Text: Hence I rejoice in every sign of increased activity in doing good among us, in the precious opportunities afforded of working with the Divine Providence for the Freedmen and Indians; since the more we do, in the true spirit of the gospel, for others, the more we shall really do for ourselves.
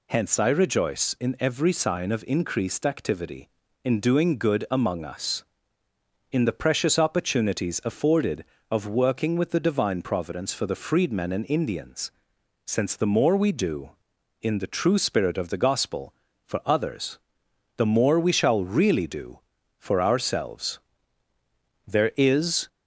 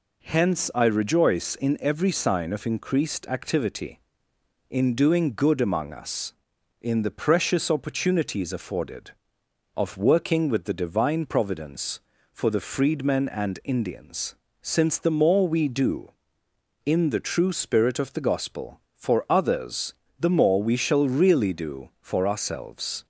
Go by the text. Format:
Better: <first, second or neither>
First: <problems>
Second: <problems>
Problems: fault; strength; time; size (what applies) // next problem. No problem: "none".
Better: second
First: goes on to say "There is"; noticeable; from 21.8 s on; 0.82 s long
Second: none